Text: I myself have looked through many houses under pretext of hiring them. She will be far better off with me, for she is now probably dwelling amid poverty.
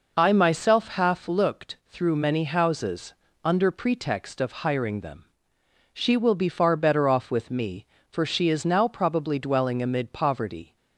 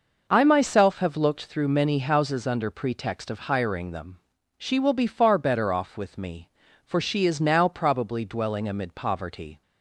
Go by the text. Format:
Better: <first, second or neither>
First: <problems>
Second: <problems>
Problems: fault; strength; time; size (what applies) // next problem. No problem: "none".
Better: second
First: says "half" for "have"; at 0.8 s // pauses between "houses" and "under"; slight; at 3.1 s; 0.30 s long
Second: none